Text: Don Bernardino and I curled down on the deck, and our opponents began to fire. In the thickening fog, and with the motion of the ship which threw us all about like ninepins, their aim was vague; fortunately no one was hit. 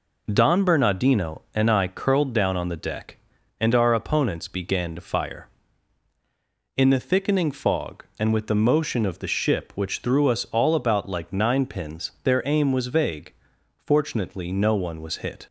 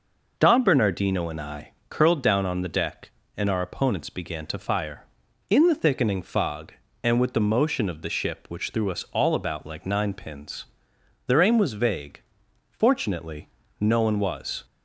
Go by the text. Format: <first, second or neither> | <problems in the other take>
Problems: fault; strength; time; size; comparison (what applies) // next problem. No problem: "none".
first | pauses between "I" and "curled"; slight; at 1.7 s; 0.18 s long // pauses between "fortunately" and "no"; slight; at 13.4 s; 0.32 s long // stops before "hit"; at 14.6 s